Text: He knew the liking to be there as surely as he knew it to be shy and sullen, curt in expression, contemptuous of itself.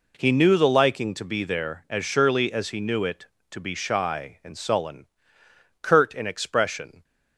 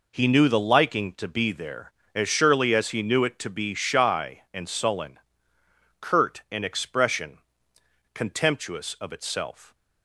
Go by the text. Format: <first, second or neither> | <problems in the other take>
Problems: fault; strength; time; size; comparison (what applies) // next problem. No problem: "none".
second | stops before "contemptuous of itself"; at 7.0 s